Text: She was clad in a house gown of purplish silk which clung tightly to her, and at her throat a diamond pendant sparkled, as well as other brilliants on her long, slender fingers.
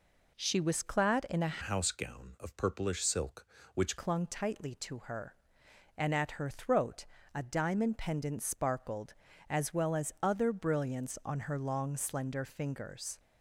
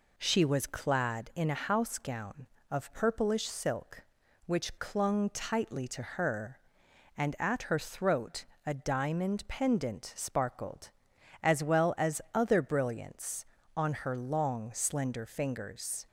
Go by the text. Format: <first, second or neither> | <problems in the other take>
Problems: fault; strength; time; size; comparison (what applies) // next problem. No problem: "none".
second | changes voice from "house" to "which"; from 1.6 to 3.9 s; 2.3 s long // pauses between "throat" and "a"; slight; at 7.0 s; 0.26 s long; slight in the second